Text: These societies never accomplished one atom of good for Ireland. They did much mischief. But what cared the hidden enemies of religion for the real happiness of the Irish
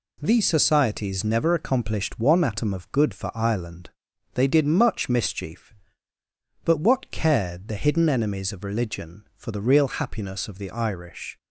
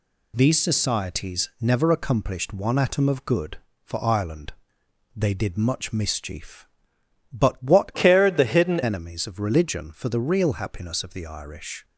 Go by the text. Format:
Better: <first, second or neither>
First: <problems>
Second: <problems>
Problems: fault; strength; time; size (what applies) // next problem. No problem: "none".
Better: first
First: none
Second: changes voice from "cared" to "hidden"; from 7.9 to 8.7 s; 0.8 s long